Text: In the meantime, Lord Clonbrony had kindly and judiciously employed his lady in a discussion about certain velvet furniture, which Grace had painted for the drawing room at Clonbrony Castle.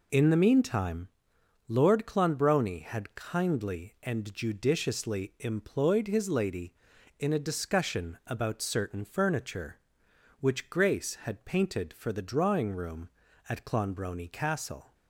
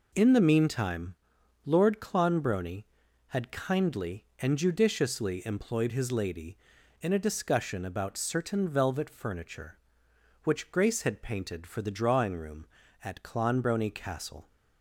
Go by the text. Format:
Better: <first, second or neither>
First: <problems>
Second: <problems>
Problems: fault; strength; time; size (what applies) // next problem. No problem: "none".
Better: second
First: skips "velvet"; at 9.0 s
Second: none